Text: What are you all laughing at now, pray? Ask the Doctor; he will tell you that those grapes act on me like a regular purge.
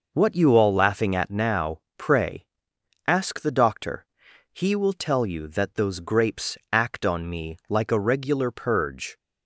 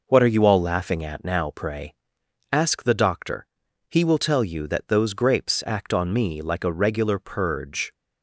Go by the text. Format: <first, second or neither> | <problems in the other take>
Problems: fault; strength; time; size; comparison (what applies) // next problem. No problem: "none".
second | skips "are"; at 0.3 s // pauses between "grapes" and "act"; slight; at 6.5 s; 0.16 s long